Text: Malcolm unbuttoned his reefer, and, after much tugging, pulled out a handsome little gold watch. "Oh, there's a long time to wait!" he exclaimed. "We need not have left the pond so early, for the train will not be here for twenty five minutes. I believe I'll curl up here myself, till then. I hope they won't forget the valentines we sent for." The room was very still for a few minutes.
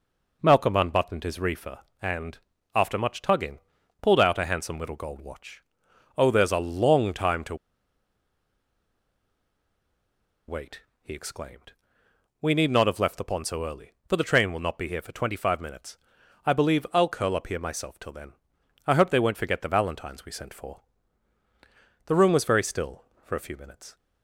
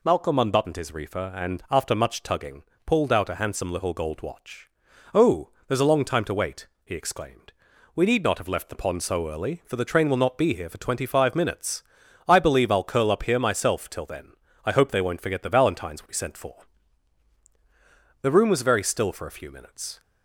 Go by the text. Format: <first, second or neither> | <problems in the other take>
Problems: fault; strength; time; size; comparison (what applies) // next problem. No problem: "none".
second | pauses between "to" and "wait"; strong; at 7.5 s; 2.9 s long